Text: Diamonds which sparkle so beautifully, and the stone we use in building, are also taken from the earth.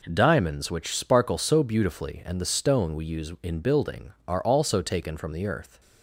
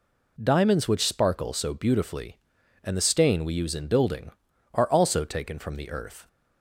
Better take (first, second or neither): first